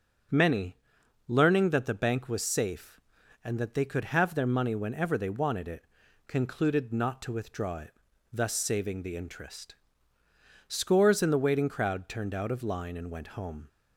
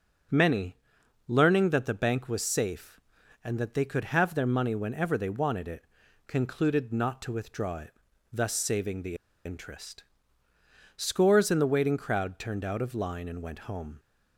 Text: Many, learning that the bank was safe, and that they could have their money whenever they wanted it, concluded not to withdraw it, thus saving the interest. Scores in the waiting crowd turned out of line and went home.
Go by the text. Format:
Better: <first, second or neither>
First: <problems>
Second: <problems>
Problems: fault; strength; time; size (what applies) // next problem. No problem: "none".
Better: first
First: starts louder than the rest; strong; until 1.8 s; 7.5 dB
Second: starts louder than the rest; strong; until 1.8 s; 7.5 dB // pauses between "the" and "interest"; slight; at 9.1 s; 0.28 s long